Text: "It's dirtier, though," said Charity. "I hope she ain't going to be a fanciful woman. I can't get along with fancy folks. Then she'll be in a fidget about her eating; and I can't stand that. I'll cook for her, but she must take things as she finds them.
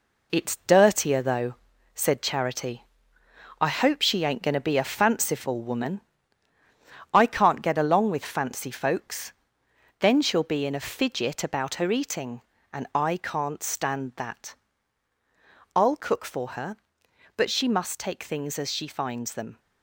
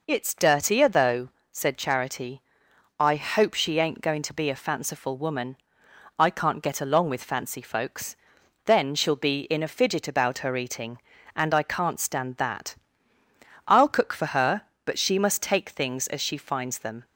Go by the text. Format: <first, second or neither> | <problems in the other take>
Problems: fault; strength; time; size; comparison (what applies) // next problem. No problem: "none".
second | gets quieter; noticeable; throughout; 6 dB